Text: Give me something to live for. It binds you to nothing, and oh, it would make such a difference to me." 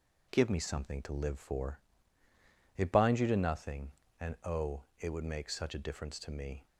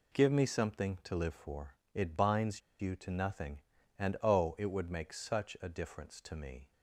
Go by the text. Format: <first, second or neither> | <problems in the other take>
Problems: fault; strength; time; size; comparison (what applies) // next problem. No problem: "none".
first | pauses between "binds" and "you"; slight; at 2.6 s; 0.19 s long